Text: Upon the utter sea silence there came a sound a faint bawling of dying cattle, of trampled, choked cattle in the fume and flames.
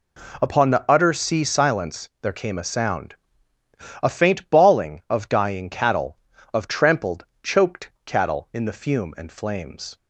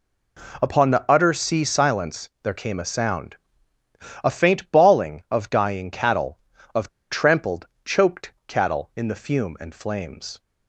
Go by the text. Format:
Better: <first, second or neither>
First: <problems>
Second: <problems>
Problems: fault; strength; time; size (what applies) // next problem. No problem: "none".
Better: first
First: pauses between "sound" and "a"; noticeable; at 3.1 s; 0.86 s long // pauses between "choked" and "cattle"; slight; at 7.9 s; 0.16 s long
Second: pauses between "sound" and "a"; noticeable; at 3.3 s; 0.86 s long // pauses between "of" and "trampled"; slight; at 6.8 s; 0.22 s long // pauses between "choked" and "cattle"; slight; at 8.3 s; 0.16 s long